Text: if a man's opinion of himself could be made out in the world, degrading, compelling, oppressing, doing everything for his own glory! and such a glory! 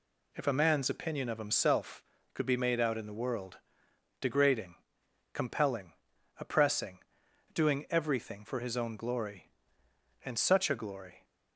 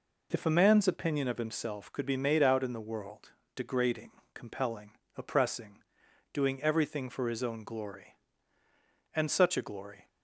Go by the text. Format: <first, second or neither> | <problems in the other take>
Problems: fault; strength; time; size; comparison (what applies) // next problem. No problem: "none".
neither | none